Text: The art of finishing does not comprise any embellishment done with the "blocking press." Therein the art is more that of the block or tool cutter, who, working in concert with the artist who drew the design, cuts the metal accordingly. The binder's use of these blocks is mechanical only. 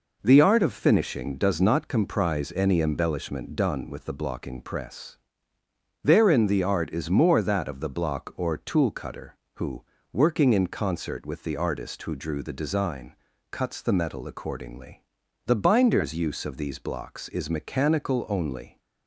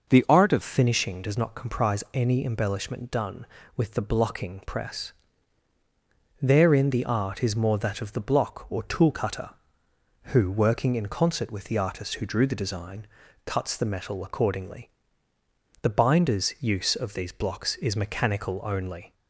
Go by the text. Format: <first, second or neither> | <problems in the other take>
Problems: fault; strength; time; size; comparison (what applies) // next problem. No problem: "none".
first | changes voice at "finishing"; from 0.6 s on; 18.5 s long